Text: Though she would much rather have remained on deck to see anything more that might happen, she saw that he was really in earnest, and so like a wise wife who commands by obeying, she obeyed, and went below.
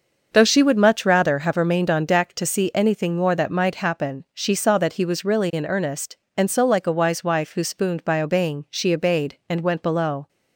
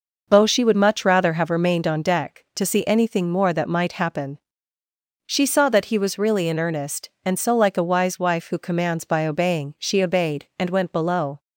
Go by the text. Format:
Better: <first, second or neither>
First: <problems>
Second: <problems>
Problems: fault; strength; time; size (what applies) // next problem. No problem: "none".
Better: second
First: starts louder than the rest; until 1.3 s; 6.5 dB // says "spooned" for "commands"; at 7.6 s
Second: none